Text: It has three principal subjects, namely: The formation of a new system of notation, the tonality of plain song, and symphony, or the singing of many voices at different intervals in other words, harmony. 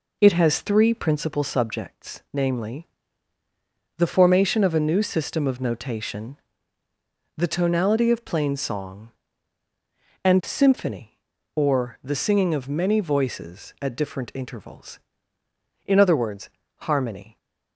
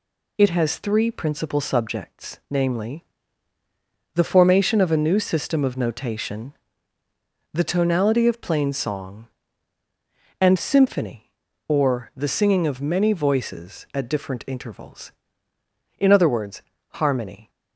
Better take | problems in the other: second | starts louder than the rest; noticeable; until 1.3 s; 4 dB

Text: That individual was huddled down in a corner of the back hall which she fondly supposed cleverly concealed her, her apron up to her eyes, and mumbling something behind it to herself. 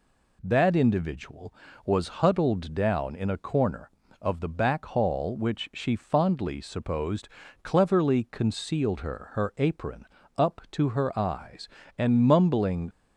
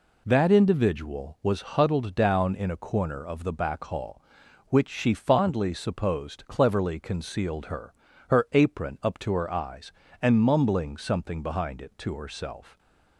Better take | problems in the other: second | pauses between "supposed" and "cleverly"; slight; at 7.2 s; 0.34 s long // pauses between "apron" and "up"; slight; at 10.0 s; 0.32 s long // stops before "something behind it to herself"; at 12.9 s

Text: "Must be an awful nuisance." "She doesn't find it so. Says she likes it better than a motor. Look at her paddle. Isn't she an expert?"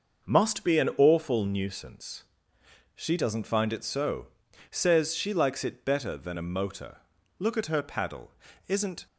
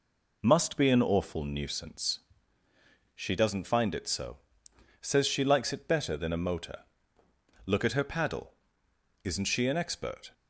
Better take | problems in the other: second | starts louder than the rest; until 1.3 s; 6 dB // stops before "she an expert"; at 9.0 s

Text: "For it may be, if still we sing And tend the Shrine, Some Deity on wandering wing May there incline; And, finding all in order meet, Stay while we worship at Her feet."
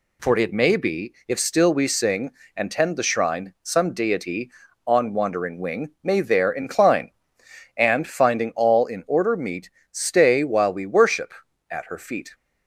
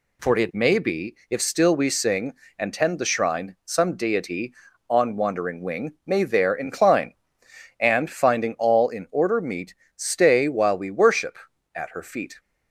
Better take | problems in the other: neither | none

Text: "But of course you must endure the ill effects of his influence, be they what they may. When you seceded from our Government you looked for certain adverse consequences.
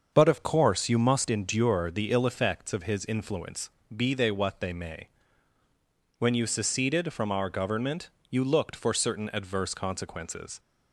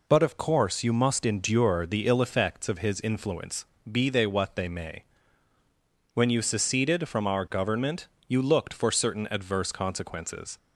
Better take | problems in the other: second | starts louder than the rest; until 1.3 s; 6.5 dB // pauses between "Government" and "you"; slight; at 8.0 s; 0.20 s long; slight in the second

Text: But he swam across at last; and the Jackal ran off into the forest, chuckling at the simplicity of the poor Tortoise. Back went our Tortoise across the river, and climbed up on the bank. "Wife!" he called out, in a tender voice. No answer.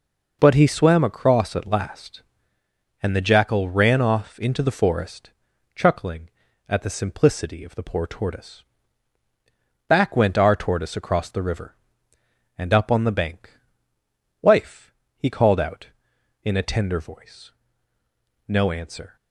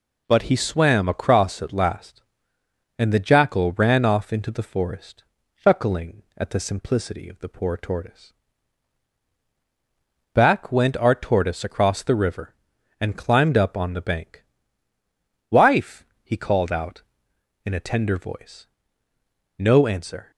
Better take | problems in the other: second | skips "climbed"; at 12.7 s

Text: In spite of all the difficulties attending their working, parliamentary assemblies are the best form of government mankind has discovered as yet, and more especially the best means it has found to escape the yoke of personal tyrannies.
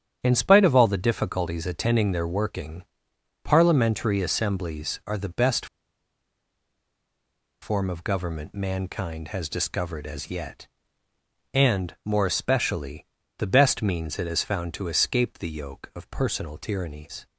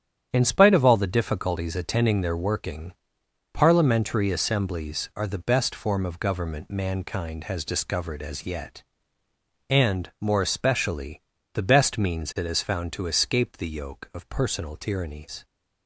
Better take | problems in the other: second | starts louder than the rest; strong; until 1.2 s; 9 dB; strong in the second // pauses between "best" and "form"; strong; at 5.6 s; 1.9 s long // pauses between "especially" and "the"; slight; at 13.0 s; 0.32 s long; slight in the second

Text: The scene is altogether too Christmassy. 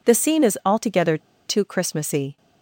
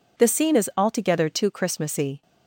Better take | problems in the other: second | pauses between "altogether" and "too"; slight; at 1.1 s; 0.27 s long

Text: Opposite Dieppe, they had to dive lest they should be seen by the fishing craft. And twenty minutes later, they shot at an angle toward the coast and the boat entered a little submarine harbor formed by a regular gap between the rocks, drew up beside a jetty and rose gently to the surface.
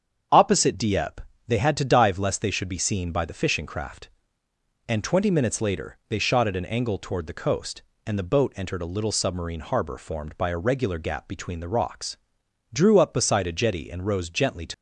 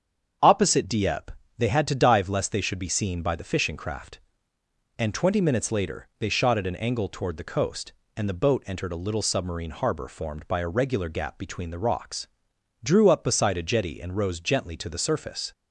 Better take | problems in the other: second | starts louder than the rest; strong; until 1.5 s; 7.5 dB; strong in the second // stops before "the surface"; at 14.7 s

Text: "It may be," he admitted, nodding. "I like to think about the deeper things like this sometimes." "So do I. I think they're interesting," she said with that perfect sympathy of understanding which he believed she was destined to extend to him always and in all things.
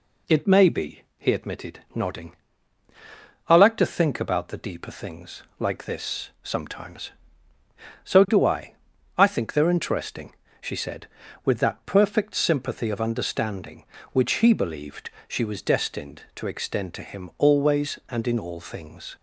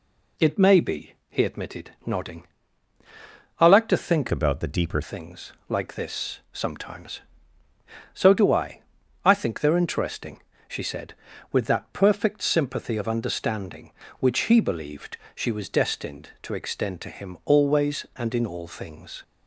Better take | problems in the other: first | changes voice from "about" to "deeper"; from 4.3 to 5.0 s; 0.7 s long // pauses between "things" and "like"; slight; at 5.5 s; 0.16 s long; slight in the first // pauses between "believed" and "she"; slight; at 15.1 s; 0.20 s long; slight in the first

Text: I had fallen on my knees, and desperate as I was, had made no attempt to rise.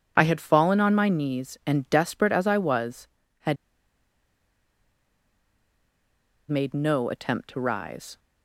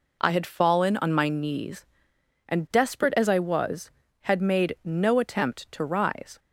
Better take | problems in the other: second | pauses between "had" and "made"; strong; at 3.5 s; 2.9 s long

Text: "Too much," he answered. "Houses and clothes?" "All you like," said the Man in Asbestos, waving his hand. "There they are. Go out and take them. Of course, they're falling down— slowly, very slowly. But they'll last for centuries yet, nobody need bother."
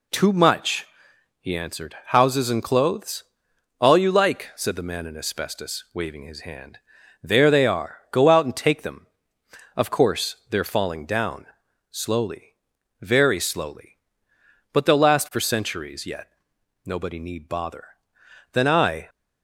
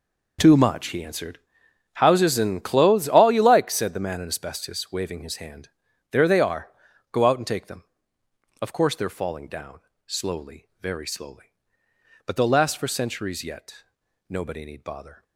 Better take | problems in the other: second | goes on to say "Then I"; from 18.5 s on; 0.56 s long

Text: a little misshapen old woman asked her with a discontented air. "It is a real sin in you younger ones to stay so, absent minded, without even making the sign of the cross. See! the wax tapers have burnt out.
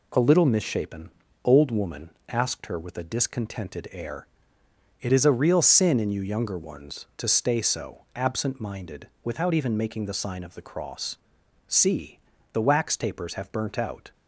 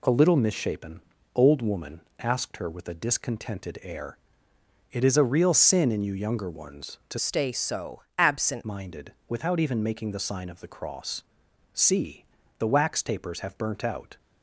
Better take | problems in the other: first | pauses between "misshapen" and "old"; slight; at 1.0 s; 0.34 s long; slight in the first // pauses between "woman" and "asked"; slight; at 1.9 s; 0.20 s long; slight in the first // changes voice from "stay" to "absent"; from 7.1 to 8.6 s; 1.5 s long

